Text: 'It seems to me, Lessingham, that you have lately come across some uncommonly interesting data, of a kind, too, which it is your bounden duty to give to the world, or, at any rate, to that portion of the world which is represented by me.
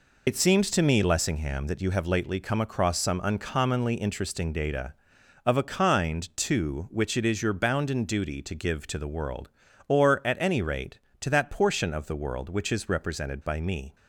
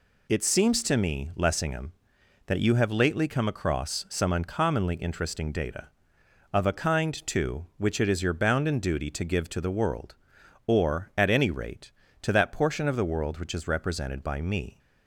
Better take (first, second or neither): second